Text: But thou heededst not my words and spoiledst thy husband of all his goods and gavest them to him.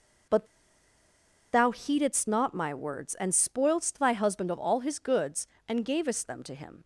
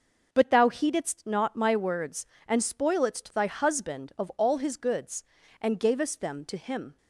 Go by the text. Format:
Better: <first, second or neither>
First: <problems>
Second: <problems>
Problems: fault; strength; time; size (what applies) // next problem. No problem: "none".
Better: second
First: pauses between "But" and "thou"; at 0.4 s; 1.0 s long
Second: none